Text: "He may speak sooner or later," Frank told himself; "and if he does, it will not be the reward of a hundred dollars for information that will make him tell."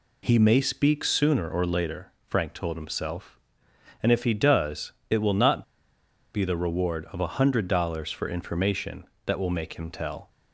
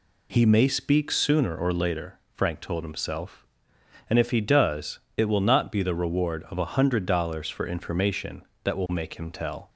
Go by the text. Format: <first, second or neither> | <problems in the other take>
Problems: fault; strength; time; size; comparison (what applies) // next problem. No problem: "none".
second | pauses between "not" and "be"; noticeable; at 5.6 s; 0.70 s long